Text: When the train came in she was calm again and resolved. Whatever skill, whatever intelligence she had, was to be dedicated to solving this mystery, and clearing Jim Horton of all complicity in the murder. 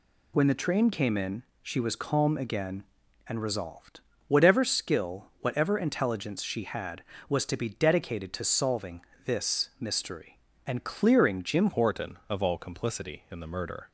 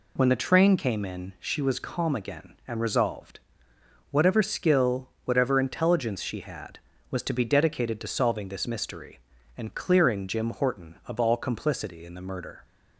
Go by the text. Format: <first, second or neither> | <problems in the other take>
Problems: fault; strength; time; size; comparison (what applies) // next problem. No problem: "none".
second | pauses between "in" and "she"; slight; at 1.4 s; 0.20 s long // pauses between "solving" and "this"; slight; at 9.0 s; 0.22 s long // changes voice at "Horton"; from 11.7 s on; 2.2 s long